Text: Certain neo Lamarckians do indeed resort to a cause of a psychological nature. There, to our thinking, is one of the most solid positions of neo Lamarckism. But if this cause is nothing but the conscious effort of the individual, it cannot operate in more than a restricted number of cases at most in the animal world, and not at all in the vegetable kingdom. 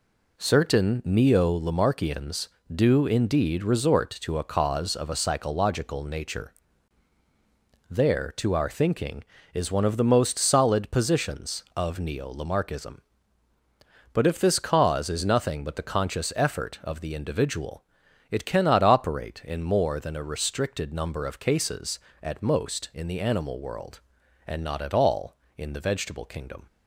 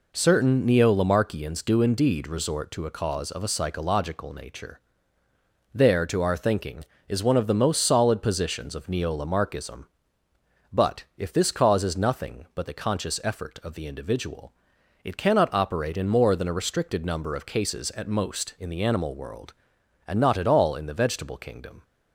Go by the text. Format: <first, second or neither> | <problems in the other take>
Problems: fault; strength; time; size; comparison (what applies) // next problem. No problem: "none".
neither | none